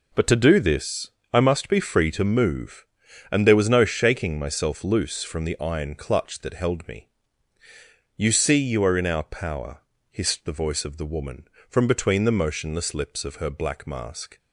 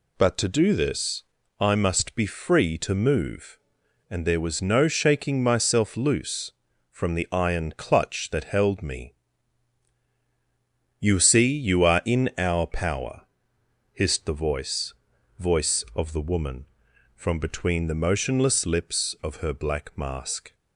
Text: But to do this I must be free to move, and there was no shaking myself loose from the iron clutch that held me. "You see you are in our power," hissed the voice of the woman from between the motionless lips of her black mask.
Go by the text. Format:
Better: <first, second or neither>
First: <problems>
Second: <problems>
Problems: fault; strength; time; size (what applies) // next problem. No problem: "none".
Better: first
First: pauses between "this" and "I"; slight; at 1.0 s; 0.22 s long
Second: pauses between "this" and "I"; at 1.2 s; 0.38 s long // says "voice" twice; at 15.3 s